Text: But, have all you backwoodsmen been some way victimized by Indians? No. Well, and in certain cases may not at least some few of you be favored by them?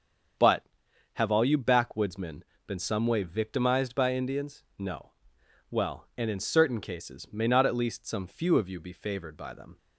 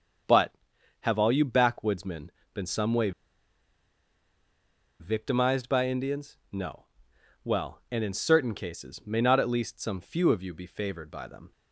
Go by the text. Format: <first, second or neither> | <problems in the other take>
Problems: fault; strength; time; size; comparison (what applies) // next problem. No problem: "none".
first | starts louder than the rest; strong; until 1.7 s; 7.5 dB; strong in the first // pauses between "backwoodsmen" and "been"; slight; at 2.2 s; 0.26 s long; slight in the first // pauses between "way" and "victimized"; strong; at 3.1 s; 1.8 s long